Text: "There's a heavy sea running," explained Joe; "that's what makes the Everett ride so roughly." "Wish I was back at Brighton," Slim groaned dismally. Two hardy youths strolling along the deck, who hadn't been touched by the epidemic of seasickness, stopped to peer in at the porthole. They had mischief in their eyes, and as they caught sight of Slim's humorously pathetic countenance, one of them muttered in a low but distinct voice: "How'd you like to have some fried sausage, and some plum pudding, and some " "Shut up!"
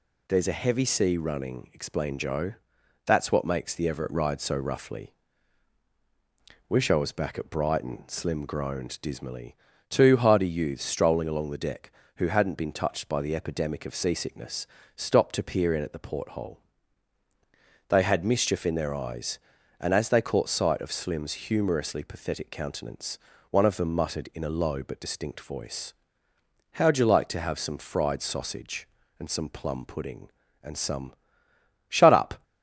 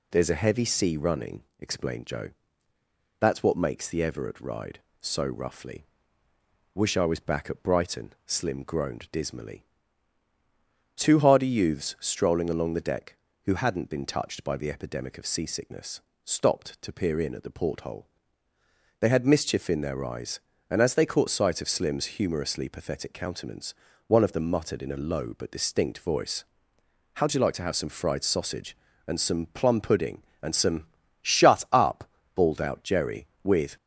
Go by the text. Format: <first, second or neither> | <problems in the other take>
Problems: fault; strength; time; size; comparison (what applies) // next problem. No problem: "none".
first | goes on to say "bawled out Jerry with"; from 32.3 s on; 1.4 s long